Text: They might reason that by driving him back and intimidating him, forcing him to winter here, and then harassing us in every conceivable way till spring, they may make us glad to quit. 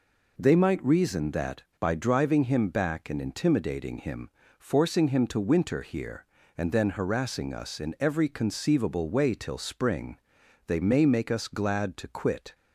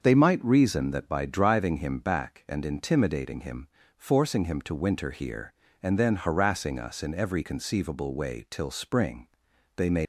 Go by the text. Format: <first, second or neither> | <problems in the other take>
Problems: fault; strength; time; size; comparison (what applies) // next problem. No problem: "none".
first | starts louder than the rest; until 1.0 s; 6.5 dB // stops before "make us glad to quit"; at 10.0 s